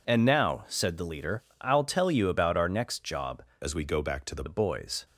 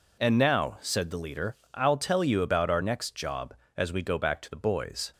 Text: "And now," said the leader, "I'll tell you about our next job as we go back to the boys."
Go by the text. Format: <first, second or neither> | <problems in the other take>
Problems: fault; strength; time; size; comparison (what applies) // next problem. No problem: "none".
second | changes voice from "as" to "the"; from 3.6 to 4.4 s; 0.8 s long